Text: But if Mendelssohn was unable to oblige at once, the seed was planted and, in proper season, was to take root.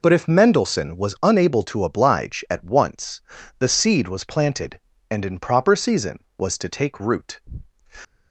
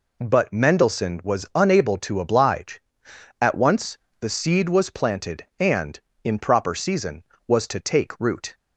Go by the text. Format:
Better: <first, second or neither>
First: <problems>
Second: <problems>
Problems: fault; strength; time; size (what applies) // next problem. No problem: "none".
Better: first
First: none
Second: skips "if"; at 0.5 s